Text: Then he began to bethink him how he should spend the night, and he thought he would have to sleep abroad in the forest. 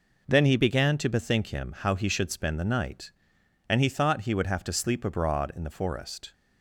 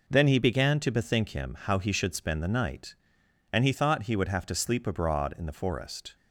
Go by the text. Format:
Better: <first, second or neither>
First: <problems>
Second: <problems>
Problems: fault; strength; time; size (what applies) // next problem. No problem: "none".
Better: neither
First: none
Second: none